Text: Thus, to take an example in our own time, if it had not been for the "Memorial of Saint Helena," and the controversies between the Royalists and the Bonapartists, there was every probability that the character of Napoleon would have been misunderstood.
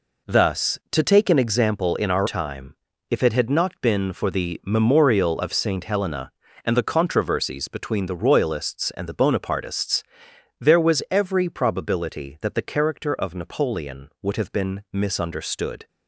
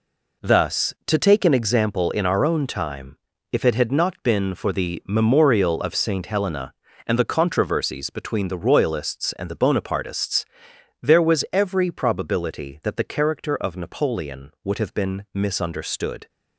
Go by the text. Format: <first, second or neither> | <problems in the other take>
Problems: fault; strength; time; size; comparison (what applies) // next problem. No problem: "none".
second | skips "own"; at 2.2 s